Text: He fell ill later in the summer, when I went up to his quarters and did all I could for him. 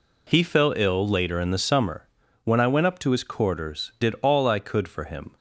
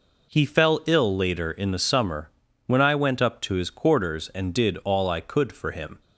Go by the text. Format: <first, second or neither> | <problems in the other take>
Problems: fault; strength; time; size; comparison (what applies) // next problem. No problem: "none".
second | skips "and"; at 3.9 s